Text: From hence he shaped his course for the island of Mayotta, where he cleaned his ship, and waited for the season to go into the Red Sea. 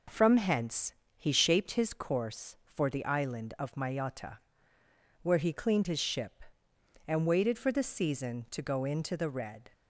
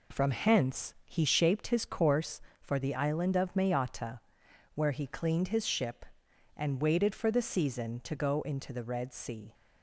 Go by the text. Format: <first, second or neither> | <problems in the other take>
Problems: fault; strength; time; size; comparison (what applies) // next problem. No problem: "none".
second | pauses between "hence" and "he"; slight; at 0.9 s; 0.22 s long // stops before "Sea"; at 9.7 s